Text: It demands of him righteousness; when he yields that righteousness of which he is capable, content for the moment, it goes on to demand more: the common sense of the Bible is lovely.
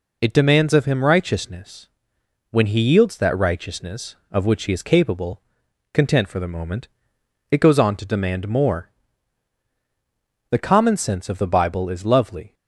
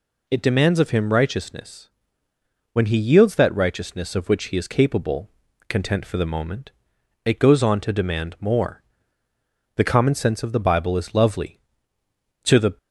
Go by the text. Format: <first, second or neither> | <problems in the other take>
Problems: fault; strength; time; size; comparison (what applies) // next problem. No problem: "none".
first | goes on to say "To the"; slight; from 12.4 s on; 0.34 s long